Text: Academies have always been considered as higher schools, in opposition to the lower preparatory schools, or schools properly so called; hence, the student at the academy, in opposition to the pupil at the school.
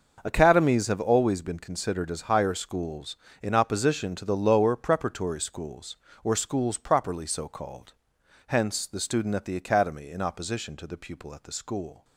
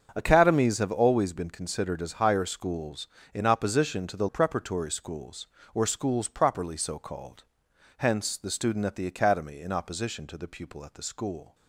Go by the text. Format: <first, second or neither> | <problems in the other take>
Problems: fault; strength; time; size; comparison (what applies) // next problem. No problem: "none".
first | starts louder than the rest; until 1.1 s; 7 dB; also in the first // skips "lower"; at 4.2 s